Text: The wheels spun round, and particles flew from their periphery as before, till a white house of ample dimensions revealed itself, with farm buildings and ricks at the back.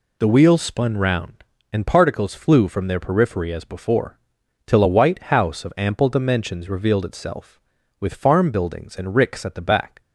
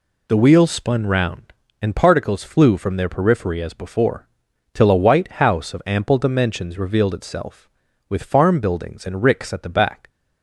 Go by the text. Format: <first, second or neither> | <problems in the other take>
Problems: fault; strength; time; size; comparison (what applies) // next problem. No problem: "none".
neither | none